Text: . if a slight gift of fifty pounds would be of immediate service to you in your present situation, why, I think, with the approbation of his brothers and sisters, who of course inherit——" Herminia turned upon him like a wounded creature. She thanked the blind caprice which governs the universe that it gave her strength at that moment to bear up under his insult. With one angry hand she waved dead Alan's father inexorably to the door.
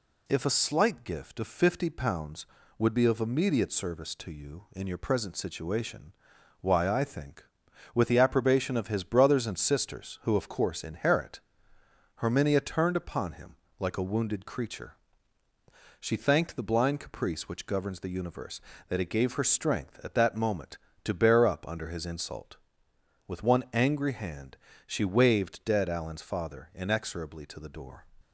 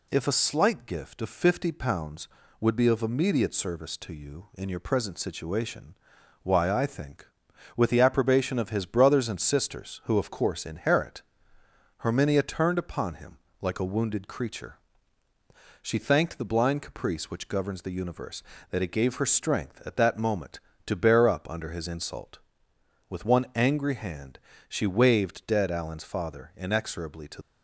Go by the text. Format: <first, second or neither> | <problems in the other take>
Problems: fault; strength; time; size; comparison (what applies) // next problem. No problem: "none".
first | pauses between "him" and "like"; slight; at 13.3 s; 0.24 s long; slight in the first // pauses between "hand" and "she"; slight; at 24.3 s; 0.28 s long; slight in the first // stops before "the door"; at 27.4 s